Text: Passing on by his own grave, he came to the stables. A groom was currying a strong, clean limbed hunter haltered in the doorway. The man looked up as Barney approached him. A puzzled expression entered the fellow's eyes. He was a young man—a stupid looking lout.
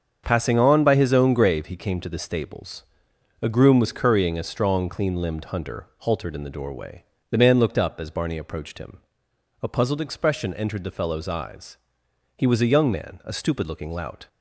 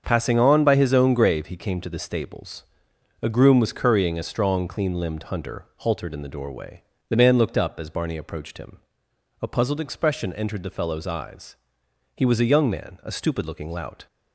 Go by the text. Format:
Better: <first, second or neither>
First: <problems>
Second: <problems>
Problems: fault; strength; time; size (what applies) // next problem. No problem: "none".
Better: neither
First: starts louder than the rest; until 1.2 s; 7 dB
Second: starts louder than the rest; until 1.0 s; 7 dB